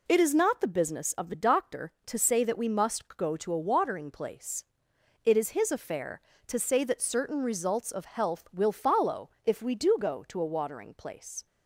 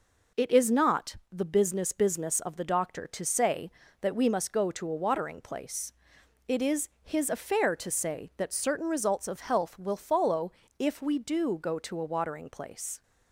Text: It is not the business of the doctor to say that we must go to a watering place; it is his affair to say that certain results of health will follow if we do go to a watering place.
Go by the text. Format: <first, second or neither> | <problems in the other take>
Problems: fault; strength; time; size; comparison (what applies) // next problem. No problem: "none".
first | says "business" twice; at 1.9 s // pauses between "follow" and "if"; slight; at 10.5 s; 0.28 s long; slight in the first